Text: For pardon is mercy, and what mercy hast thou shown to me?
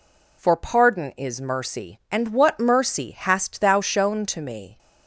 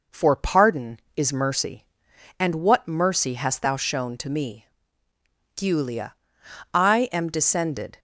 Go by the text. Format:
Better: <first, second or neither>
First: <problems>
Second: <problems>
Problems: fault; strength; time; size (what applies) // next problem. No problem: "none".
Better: first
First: none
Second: goes on to say "Giulia I am descended"; strong; from 5.5 s on; 2.4 s long